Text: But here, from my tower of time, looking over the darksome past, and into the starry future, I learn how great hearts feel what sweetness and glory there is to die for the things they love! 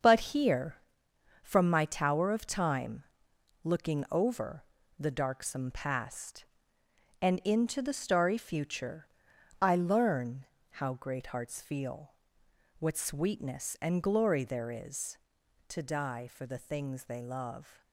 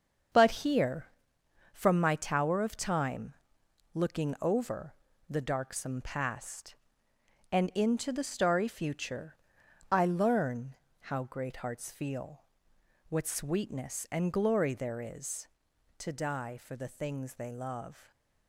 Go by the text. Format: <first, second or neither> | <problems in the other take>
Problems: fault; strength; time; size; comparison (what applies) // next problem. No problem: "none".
neither | starts louder than the rest; strong; the same in both // pauses between "over" and "the"; slight; the same in both // pauses between "learn" and "how"; slight; the same in both // pauses between "feel" and "what"; noticeable; the same in both